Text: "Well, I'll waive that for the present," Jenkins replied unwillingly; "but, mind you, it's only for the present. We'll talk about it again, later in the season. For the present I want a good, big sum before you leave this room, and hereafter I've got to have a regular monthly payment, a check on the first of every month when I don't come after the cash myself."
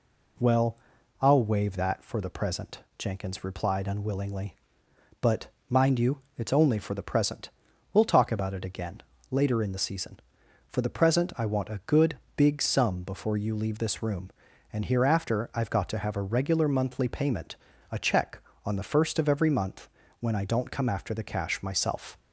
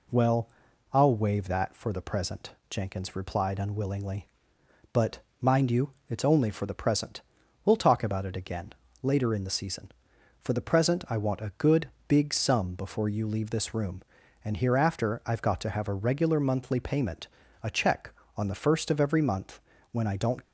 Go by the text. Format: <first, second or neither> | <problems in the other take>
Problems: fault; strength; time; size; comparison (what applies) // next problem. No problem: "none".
first | pauses between "month" and "when"; slight; at 19.6 s; 0.30 s long; slight in the first // stops before "come after the cash myself"; at 20.4 s